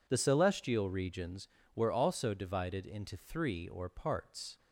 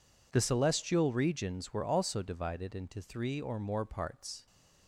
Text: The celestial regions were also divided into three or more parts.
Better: second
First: skips "more"; at 3.8 s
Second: none

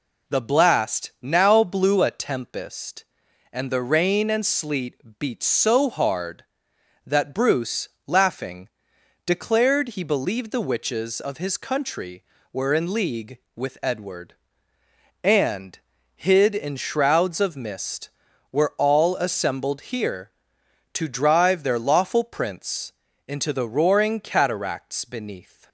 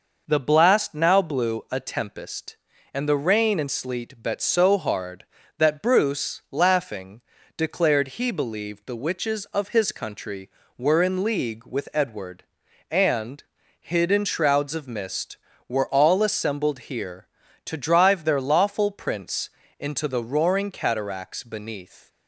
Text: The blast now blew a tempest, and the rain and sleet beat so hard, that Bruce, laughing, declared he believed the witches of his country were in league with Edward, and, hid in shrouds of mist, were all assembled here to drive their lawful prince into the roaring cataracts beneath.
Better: first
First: pauses between "prince" and "into"; at 22.9 s; 0.38 s long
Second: says "bet" for "beat"; at 4.2 s // pauses between "prince" and "into"; slight; at 19.4 s; 0.30 s long

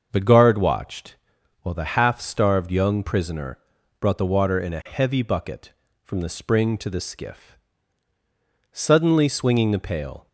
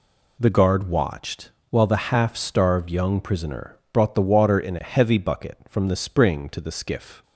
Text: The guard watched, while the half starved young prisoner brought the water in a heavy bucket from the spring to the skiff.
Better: second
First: starts louder than the rest; until 1.1 s; 6.5 dB // pauses between "prisoner" and "brought"; at 3.5 s; 0.42 s long // goes on to say "Suddenly swinging the pail"; from 8.7 s on; 1.5 s long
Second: pauses between "prisoner" and "brought"; slight; at 3.7 s; 0.16 s long

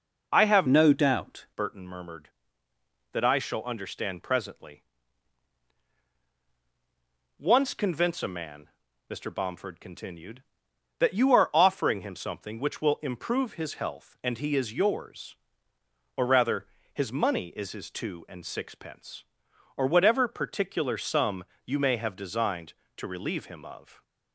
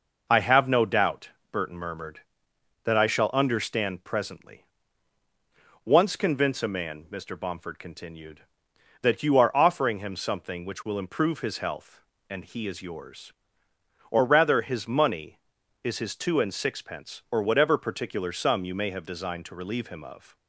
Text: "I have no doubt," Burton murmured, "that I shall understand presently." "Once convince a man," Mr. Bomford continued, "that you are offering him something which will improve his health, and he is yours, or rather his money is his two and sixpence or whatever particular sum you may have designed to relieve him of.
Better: second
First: changes voice from "no" to "doubt"; from 0.6 to 1.4 s; 0.8 s long // pauses between "rather" and "his"; slight; at 16.6 s; 0.28 s long // pauses between "sum" and "you"; slight; at 21.4 s; 0.20 s long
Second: none

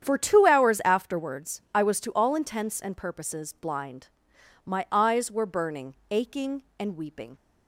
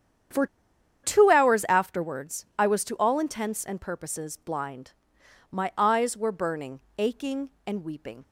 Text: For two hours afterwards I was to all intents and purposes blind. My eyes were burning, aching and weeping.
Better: first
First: starts louder than the rest; strong; until 1.0 s; 9 dB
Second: starts louder than the rest; strong; until 1.9 s; 9 dB // pauses between "For" and "two"; noticeable; at 0.4 s; 0.58 s long

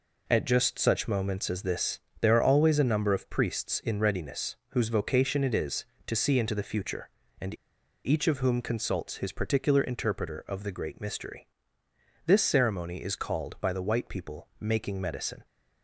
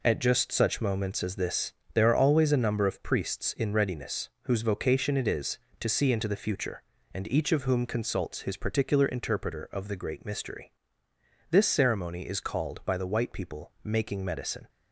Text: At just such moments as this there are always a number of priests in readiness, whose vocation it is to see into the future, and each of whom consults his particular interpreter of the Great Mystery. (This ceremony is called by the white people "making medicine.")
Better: second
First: pauses between "this" and "there"; slight; at 2.0 s; 0.20 s long // pauses between "and" and "each"; noticeable; at 7.5 s; 0.48 s long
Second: pauses between "this" and "there"; slight; at 1.7 s; 0.20 s long

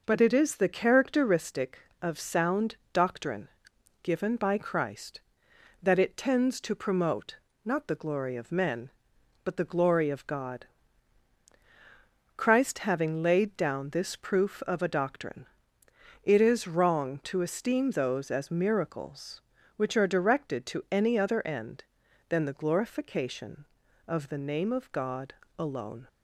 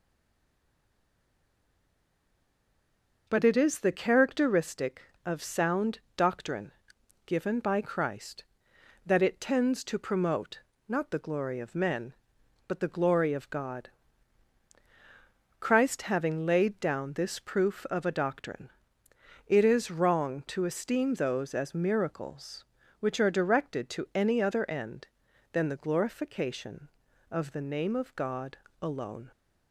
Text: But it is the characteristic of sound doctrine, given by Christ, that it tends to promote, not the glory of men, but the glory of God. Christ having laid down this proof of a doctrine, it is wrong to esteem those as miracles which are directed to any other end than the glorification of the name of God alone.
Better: first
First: pauses between "sound" and "doctrine"; slight; at 2.7 s; 0.16 s long // pauses between "God" and "alone"; slight; at 25.3 s; 0.24 s long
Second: stays silent before the first word; strong; until 3.2 s; 3.2 s long // pauses between "sound" and "doctrine"; slight; at 5.9 s; 0.16 s long // pauses between "God" and "alone"; slight; at 28.5 s; 0.24 s long

